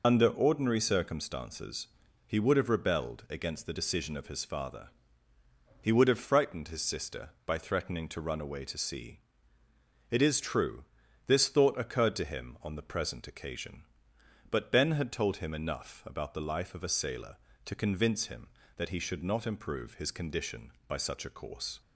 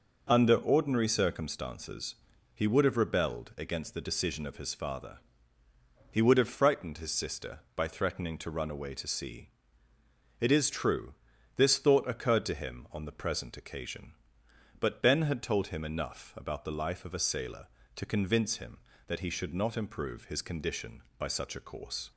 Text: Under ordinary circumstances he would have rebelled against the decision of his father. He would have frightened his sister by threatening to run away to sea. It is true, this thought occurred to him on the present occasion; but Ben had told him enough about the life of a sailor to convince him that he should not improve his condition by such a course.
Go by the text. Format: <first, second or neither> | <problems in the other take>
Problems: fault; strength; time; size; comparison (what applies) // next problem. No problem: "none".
second | loses the start of "Under"; at 0.0 s; 55 ms // pauses between "circumstances" and "he"; at 1.8 s; 0.38 s long; also in the second